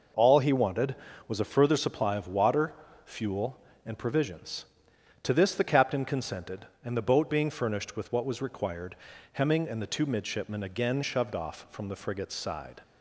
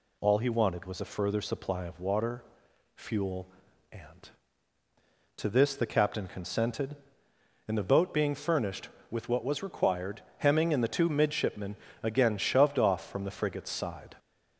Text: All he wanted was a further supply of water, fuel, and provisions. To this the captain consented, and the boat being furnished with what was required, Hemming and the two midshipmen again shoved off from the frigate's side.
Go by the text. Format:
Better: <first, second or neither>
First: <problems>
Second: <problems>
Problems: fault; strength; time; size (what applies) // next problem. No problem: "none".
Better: first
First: none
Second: skips "provisions"; at 4.8 s // pauses between "midshipmen" and "again"; slight; at 11.7 s; 0.26 s long